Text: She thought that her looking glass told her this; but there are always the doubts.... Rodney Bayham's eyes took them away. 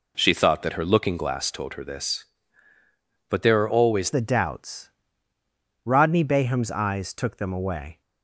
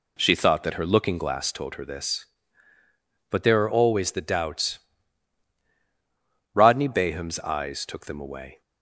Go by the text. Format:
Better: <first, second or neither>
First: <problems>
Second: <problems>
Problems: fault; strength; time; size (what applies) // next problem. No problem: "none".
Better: second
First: changes voice at "the"; from 4.1 s on; 3.9 s long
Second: none